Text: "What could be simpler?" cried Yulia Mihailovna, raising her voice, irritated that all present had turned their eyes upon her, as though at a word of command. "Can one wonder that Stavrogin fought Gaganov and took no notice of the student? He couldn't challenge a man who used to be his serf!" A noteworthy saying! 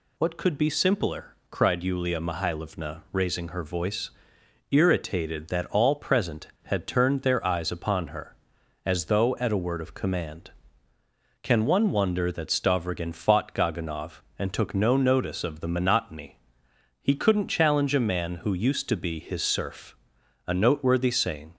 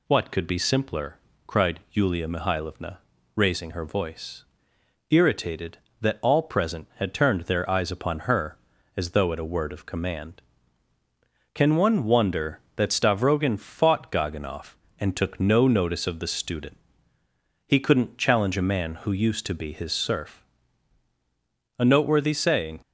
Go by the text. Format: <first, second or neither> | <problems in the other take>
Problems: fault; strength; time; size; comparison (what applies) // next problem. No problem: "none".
second | says "monotony" for "student"; at 15.6 s